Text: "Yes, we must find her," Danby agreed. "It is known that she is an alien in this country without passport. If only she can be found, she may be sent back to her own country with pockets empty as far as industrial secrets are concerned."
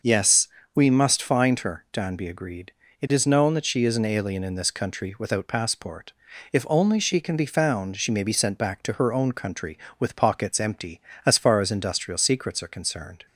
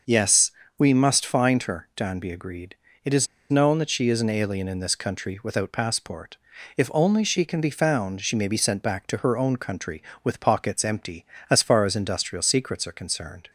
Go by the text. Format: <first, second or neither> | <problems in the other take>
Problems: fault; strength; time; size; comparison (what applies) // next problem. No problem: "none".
first | pauses between "is" and "known"; slight; at 3.2 s; 0.23 s long